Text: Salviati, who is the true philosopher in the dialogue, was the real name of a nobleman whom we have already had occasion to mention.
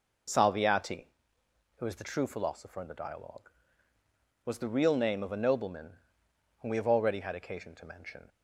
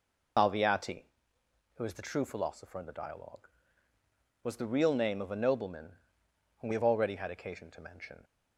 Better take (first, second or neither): first